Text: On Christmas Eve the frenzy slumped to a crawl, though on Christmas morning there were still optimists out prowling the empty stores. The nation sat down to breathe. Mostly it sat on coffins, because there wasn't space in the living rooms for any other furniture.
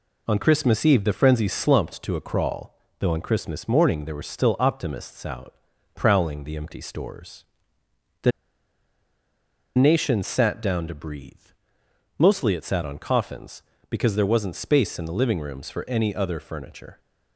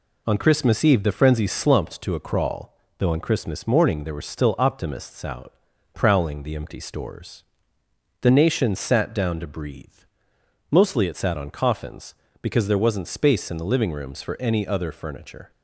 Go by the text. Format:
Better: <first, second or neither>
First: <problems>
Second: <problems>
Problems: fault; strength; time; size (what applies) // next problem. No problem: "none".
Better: second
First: pauses between "out" and "prowling"; at 5.5 s; 0.42 s long // pauses between "The" and "nation"; strong; at 8.3 s; 1.4 s long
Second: pauses between "out" and "prowling"; at 5.5 s; 0.42 s long